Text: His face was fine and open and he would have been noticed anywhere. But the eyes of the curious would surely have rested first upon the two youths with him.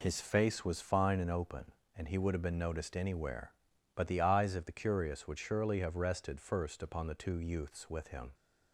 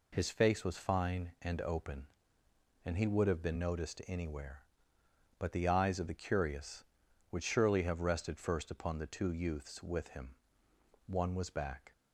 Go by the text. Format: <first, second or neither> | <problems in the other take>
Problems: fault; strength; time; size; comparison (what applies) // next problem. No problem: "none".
first | goes on to say "One was back"; noticeable; from 11.0 s on; 0.86 s long